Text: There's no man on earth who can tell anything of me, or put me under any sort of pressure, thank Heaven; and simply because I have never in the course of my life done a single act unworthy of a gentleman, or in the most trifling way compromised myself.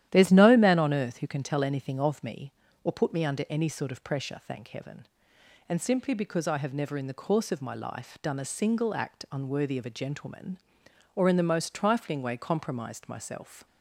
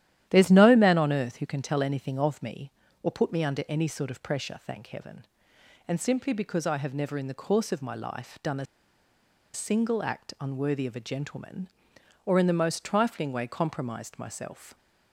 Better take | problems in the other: first | starts louder than the rest; strong; until 1.3 s; 12 dB; strong in the first // pauses between "a" and "single"; noticeable; at 8.6 s; 0.88 s long

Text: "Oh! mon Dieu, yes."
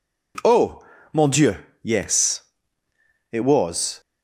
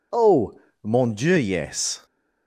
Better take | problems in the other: second | goes on to say "It was"; noticeable; from 3.3 s on; 0.68 s long

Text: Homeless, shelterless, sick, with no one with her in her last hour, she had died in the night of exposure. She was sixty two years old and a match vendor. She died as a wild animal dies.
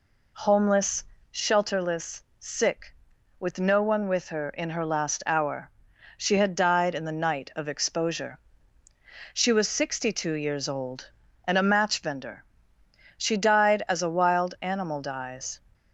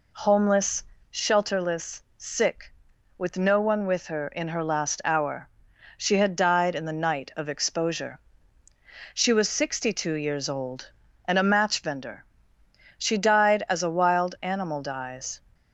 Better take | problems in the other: neither | none

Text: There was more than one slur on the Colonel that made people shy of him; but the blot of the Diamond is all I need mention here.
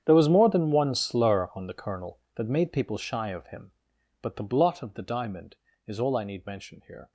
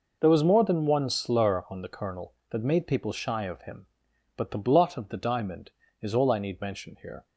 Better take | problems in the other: second | gets quieter; strong; throughout; 19.5 dB

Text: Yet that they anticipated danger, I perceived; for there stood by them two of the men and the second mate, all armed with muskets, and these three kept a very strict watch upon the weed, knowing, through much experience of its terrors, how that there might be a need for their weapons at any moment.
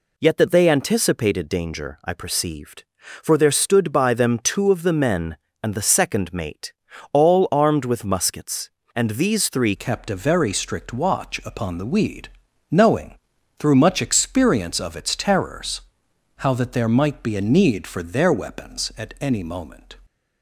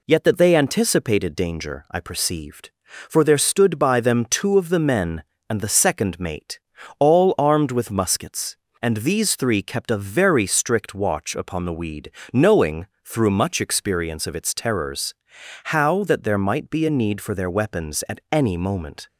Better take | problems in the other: second | changes voice at "kept"; from 9.7 s on; 10.2 s long

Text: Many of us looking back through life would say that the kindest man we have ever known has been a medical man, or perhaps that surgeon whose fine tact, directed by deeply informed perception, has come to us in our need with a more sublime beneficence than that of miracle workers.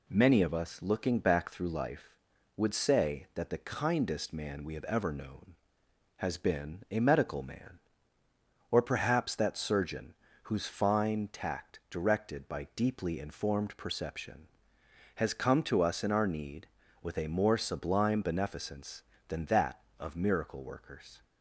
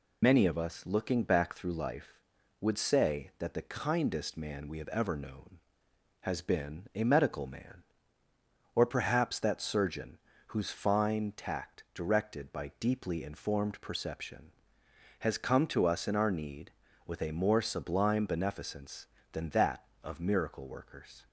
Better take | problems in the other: first | loses the start of "Many"; at 0.2 s; 95 ms // pauses between "surgeon" and "whose"; slight; at 10.1 s; 0.30 s long; slight in the first

